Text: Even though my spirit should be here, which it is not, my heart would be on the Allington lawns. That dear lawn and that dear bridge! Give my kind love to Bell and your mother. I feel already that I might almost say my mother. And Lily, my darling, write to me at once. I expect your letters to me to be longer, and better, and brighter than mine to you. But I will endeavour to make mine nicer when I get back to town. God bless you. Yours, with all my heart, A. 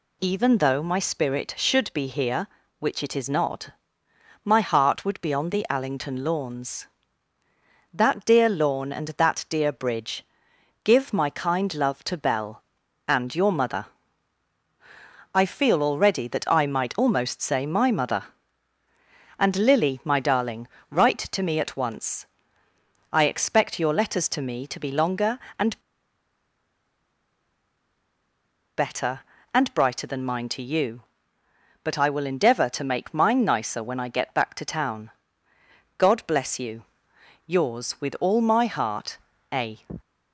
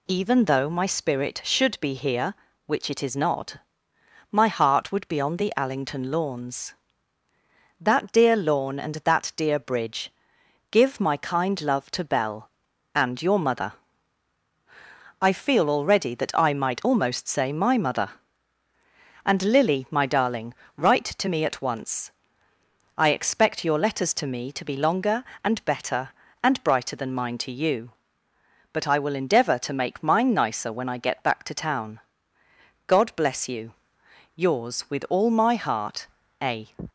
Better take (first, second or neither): second